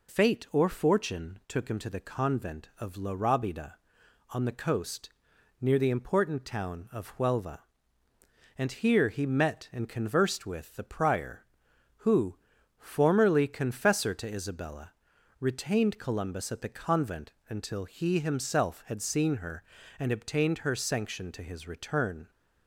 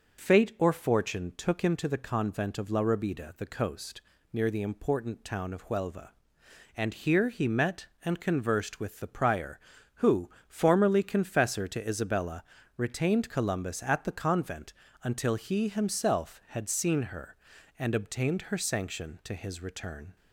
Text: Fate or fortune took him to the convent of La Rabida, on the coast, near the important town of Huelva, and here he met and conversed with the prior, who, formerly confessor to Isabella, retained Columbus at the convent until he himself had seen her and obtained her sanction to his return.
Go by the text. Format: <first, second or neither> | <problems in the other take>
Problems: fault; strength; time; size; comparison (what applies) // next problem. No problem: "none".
first | skips "on"; at 3.3 s // pauses between "convent" and "until"; slight; at 14.7 s; 0.30 s long; slight in the first